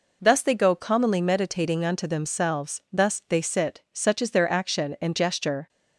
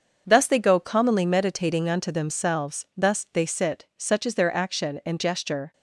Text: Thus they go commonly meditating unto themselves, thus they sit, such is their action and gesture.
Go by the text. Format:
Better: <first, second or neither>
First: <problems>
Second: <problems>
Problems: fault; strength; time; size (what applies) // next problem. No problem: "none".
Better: first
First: none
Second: gets quieter; strong; throughout; 8 dB